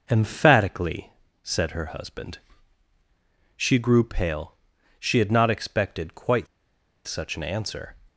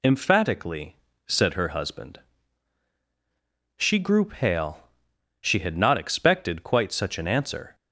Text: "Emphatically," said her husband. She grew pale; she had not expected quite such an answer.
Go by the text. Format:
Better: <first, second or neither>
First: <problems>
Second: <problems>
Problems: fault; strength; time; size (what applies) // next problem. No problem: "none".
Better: second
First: pauses between "quite" and "such"; noticeable; at 6.4 s; 0.61 s long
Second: none